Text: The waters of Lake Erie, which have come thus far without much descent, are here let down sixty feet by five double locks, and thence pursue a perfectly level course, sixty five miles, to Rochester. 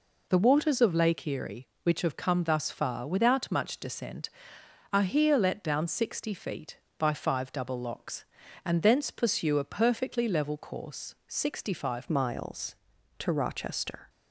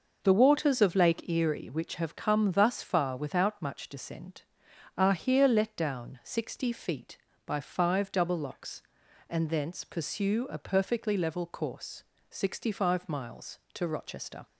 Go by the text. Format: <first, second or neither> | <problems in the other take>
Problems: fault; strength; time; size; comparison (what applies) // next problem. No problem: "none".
second | changes voice at "miles"; from 12.0 s on; 2.0 s long